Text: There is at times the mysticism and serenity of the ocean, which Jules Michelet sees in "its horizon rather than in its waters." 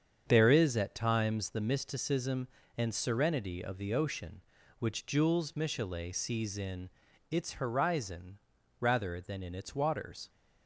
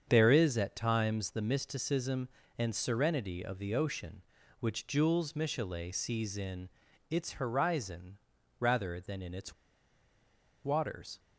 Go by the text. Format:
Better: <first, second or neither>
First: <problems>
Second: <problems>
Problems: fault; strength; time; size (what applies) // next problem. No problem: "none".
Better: first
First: starts louder than the rest; strong; until 1.2 s; 7.5 dB // pauses between "in" and "its"; at 6.9 s; 0.40 s long // pauses between "horizon" and "rather"; at 8.3 s; 0.42 s long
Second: starts louder than the rest; strong; until 1.0 s; 7.5 dB // pauses between "in" and "its"; at 6.7 s; 0.40 s long // pauses between "horizon" and "rather"; at 8.1 s; 0.42 s long // pauses between "its" and "waters"; at 9.5 s; 1.1 s long